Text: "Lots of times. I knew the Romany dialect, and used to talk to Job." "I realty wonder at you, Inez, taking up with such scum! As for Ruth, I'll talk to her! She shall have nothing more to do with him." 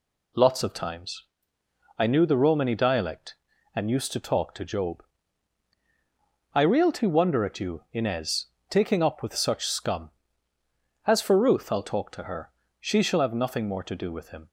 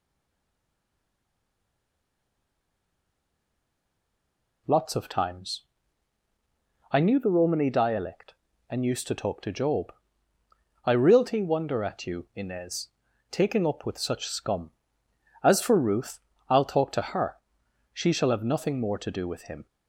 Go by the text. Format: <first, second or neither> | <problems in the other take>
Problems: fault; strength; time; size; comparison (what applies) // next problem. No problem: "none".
first | stays silent before the first word; strong; until 4.6 s; 4.6 s long